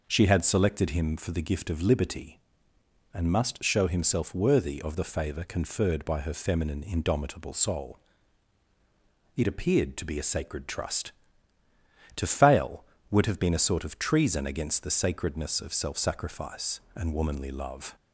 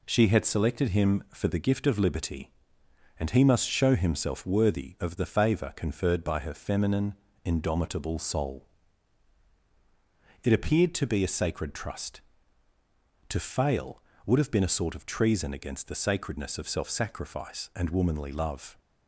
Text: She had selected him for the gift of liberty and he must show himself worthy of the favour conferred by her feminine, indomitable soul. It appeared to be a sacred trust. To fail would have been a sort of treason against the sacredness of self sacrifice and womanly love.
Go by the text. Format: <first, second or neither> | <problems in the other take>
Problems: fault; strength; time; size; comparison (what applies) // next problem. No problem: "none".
second | skips "he"; at 3.3 s